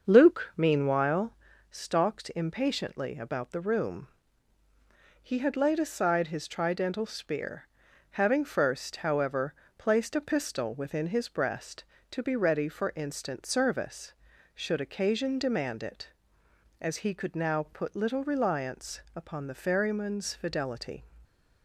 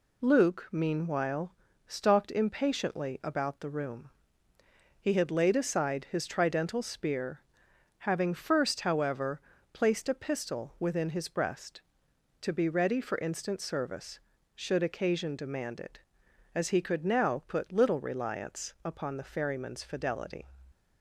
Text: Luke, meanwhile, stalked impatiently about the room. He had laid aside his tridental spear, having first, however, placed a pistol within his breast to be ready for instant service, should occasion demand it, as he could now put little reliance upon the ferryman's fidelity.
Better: second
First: starts louder than the rest; until 1.5 s; 6.5 dB // stays silent after the last word; slight; from 21.0 s on; 0.6 s long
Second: none

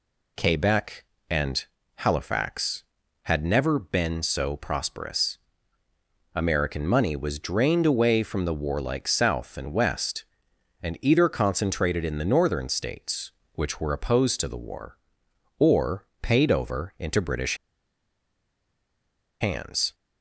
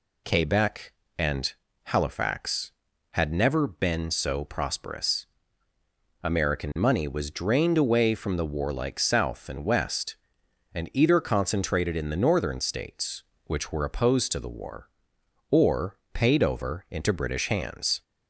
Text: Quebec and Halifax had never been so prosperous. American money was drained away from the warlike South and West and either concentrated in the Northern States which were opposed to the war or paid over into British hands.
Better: second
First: pauses between "and" and "Halifax"; slight; at 1.6 s; 0.32 s long // pauses between "or" and "paid"; slight; at 16.0 s; 0.16 s long // pauses between "British" and "hands"; strong; at 17.5 s; 1.8 s long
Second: pauses between "and" and "Halifax"; slight; at 1.5 s; 0.32 s long // pauses between "or" and "paid"; slight; at 15.9 s; 0.16 s long

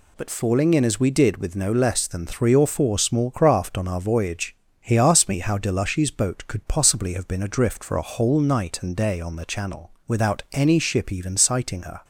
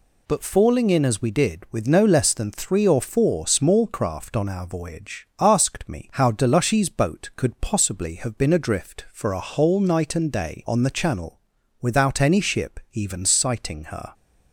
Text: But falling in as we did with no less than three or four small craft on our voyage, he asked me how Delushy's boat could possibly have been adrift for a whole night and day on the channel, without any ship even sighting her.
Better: first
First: none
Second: skips "he"; at 5.3 s

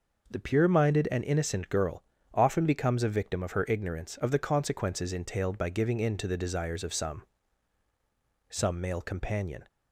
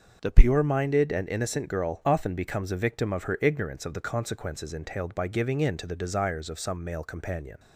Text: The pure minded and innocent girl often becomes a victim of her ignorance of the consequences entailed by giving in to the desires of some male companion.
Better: second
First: pauses between "girl" and "often"; slight; at 2.0 s; 0.32 s long // says "some" twice; at 8.4 s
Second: none

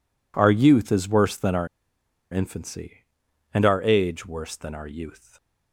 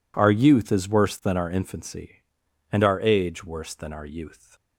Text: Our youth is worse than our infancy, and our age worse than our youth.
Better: second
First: pauses between "our" and "infancy"; noticeable; at 1.6 s; 0.65 s long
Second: none

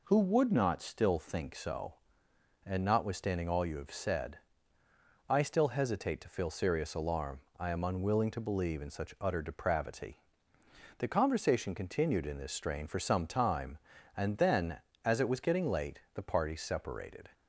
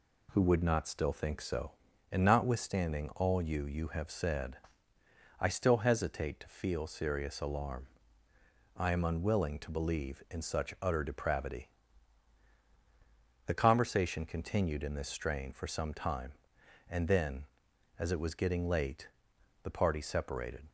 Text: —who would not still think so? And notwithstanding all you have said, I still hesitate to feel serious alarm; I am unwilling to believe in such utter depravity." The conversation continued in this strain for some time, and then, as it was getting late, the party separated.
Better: first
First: none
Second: says "you" twice; at 3.6 s

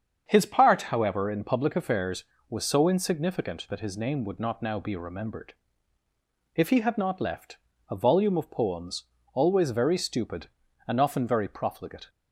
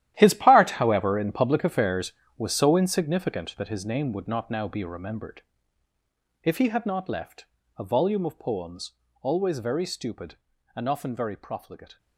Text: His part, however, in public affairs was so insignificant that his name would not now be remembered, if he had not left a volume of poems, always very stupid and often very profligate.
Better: first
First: starts louder than the rest; strong; until 1.2 s; 7.5 dB // pauses between "left" and "a"; slight; at 7.5 s; 0.32 s long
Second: gets quieter; strong; throughout; 14.5 dB // starts louder than the rest; strong; until 1.1 s; 12.5 dB // pauses between "left" and "a"; slight; at 7.4 s; 0.32 s long

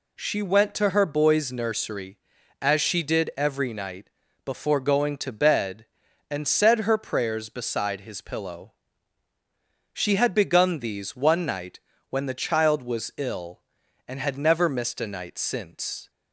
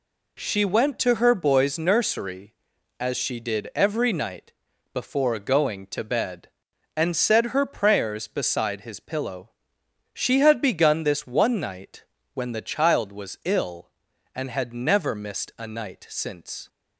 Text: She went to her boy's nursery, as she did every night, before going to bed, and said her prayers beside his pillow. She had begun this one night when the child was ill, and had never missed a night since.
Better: second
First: says "these" for "this"; at 10.7 s // pauses between "night" and "when"; slight; at 11.7 s; 0.32 s long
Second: pauses between "night" and "when"; slight; at 12.0 s; 0.30 s long

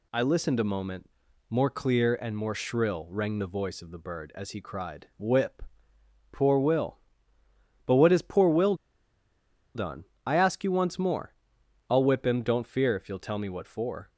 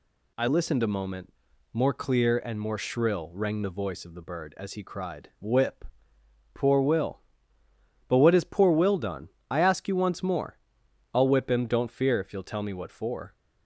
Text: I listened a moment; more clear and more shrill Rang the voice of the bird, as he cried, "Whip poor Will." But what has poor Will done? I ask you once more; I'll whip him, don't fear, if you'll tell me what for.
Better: second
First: pauses between "Whip" and "poor"; noticeable; at 5.6 s; 0.70 s long // pauses between "Will" and "done"; at 8.7 s; 1.0 s long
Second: pauses between "Whip" and "poor"; noticeable; at 5.8 s; 0.70 s long

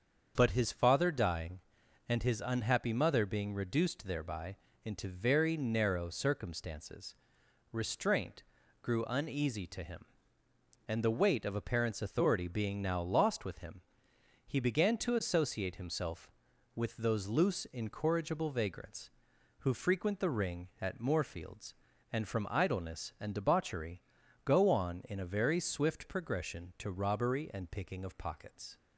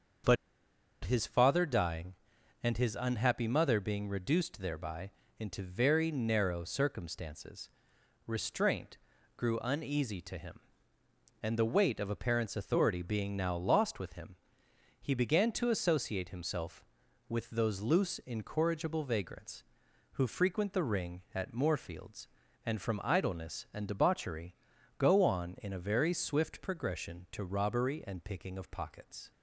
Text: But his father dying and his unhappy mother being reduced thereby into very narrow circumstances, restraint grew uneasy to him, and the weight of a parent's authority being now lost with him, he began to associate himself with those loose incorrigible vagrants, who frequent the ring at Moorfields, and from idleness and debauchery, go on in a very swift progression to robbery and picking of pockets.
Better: first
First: starts louder than the rest; until 1.3 s; 7 dB // pauses between "thereby" and "into"; slight; at 4.5 s; 0.28 s long // pauses between "restraint" and "grew"; at 8.4 s; 0.40 s long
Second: starts louder than the rest; until 1.9 s; 7 dB // pauses between "But" and "his"; noticeable; at 0.3 s; 0.68 s long // pauses between "thereby" and "into"; slight; at 5.1 s; 0.28 s long // pauses between "restraint" and "grew"; at 8.9 s; 0.40 s long

